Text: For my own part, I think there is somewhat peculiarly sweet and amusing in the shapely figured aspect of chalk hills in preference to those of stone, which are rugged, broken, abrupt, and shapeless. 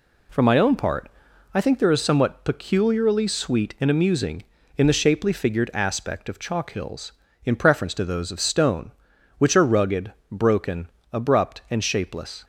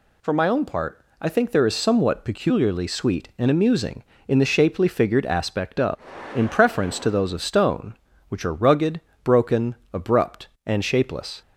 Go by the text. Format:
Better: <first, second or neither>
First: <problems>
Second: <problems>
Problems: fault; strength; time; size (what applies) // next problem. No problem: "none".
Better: first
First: none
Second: skips "chalk hills"; at 6.1 s